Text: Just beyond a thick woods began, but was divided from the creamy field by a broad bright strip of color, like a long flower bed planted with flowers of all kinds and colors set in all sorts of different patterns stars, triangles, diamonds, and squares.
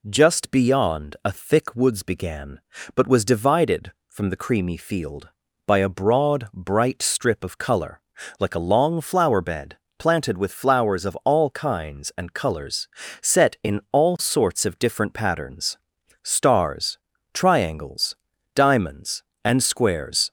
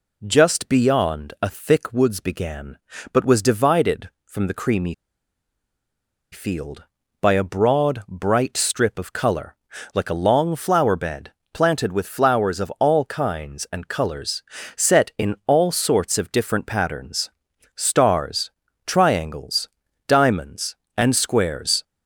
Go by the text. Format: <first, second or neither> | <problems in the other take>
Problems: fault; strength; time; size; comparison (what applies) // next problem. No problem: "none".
first | pauses between "creamy" and "field"; strong; at 4.9 s; 1.3 s long // pauses between "bed" and "planted"; slight; at 11.3 s; 0.22 s long; slight in the first // pauses between "colors" and "set"; slight; at 14.4 s; 0.34 s long; slight in the first // pauses between "patterns" and "stars"; noticeable; at 17.2 s; 0.46 s long; noticeable in the first